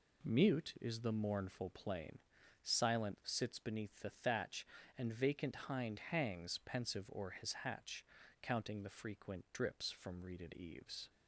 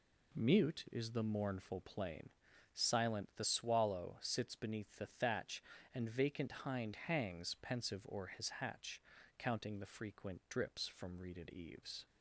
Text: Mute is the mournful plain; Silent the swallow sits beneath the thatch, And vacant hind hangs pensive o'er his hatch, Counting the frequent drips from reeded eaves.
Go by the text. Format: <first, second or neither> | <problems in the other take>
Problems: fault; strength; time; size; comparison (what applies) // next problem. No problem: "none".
second | skips "the swallow"; at 3.2 s